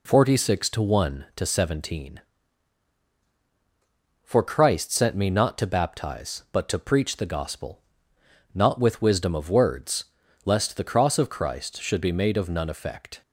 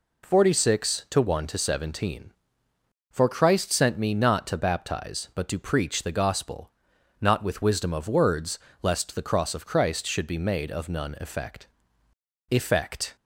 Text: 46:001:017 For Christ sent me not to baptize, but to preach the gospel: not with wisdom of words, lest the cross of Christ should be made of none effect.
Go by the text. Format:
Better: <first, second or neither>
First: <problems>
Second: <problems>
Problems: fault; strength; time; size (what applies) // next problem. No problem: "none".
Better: first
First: none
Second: says "effect" twice; at 12.4 s